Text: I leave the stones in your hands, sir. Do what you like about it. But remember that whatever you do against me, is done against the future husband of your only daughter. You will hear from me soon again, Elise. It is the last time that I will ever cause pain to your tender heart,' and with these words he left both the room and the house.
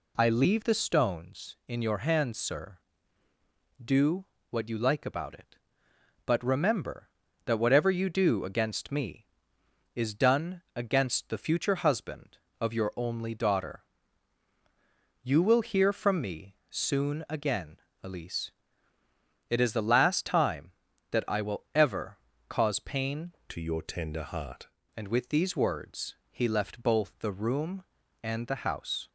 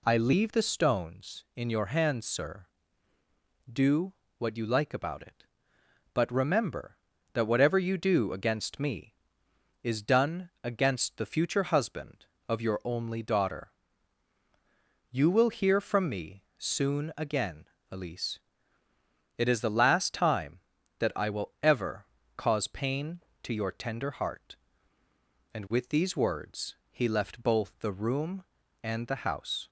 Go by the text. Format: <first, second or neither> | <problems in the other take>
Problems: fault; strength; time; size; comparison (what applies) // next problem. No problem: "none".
second | pauses between "Do" and "what"; slight; at 4.2 s; 0.24 s long; slight in the second // pauses between "ever" and "cause"; slight; at 22.1 s; 0.32 s long; slight in the second // changes voice from "to" to "heart"; from 23.4 to 24.6 s; 1.2 s long // pauses between "words" and "he"; slight; at 26.1 s; 0.16 s long; slight in the second